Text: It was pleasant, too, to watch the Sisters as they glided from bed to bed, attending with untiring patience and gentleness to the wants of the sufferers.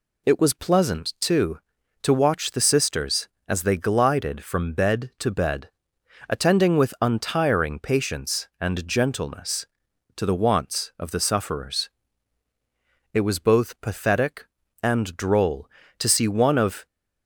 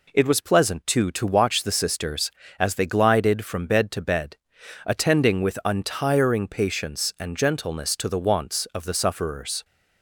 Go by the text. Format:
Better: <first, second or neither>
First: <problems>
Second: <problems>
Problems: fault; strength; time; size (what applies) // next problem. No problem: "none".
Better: second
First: goes on to say "It was both pathetic and droll to see one of"; strong; from 13.1 s on; 3.7 s long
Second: none